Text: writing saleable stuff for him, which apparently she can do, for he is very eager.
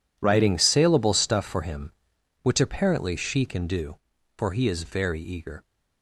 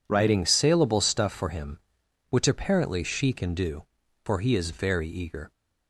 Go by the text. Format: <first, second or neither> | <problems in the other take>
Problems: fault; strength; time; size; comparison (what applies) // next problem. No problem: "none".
second | gets quieter; strong; throughout; 14.5 dB